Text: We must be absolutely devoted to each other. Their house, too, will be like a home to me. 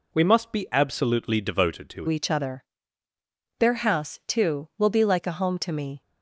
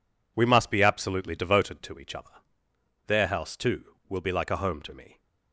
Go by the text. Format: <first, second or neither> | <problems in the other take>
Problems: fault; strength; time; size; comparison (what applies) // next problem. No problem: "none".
second | changes voice at "each"; from 2.0 s on; 4.0 s long